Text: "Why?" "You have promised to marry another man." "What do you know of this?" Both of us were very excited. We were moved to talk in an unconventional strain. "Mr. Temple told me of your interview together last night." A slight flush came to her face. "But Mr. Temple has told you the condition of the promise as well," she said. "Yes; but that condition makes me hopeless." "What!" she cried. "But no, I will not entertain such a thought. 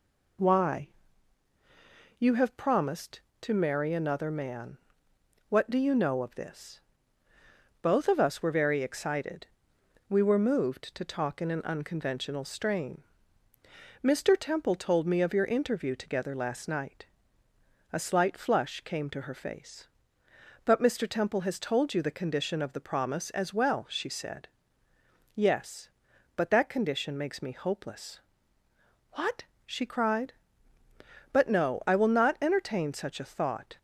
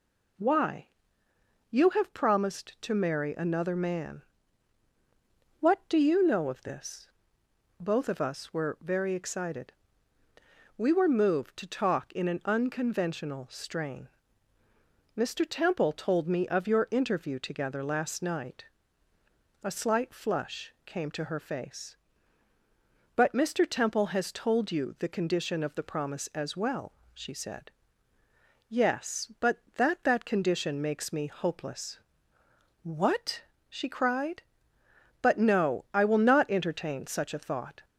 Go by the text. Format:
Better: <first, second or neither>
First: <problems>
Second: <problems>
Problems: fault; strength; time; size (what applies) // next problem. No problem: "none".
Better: first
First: none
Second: says "that" twice; at 30.0 s